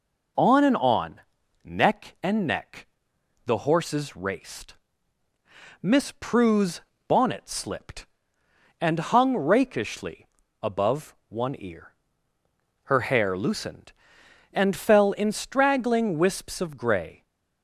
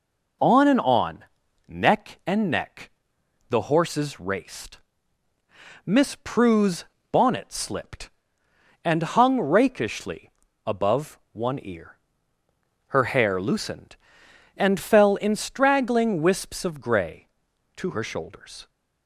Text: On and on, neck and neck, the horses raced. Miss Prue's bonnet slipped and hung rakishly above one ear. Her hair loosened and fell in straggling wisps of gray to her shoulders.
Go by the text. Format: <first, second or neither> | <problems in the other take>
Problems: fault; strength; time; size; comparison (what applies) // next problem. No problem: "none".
second | pauses between "Prue's" and "bonnet"; slight; at 6.8 s; 0.26 s long; slight in the second // pauses between "rakishly" and "above"; slight; at 10.2 s; 0.34 s long; slight in the second // stops before "to her shoulders"; at 17.2 s